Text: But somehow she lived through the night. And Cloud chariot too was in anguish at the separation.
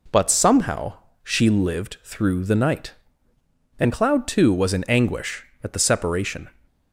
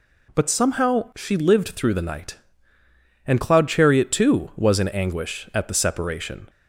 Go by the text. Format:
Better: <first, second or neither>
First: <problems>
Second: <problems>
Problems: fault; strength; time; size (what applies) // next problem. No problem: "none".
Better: second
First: pauses between "somehow" and "she"; slight; at 0.9 s; 0.28 s long // skips "chariot"; at 4.2 s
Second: none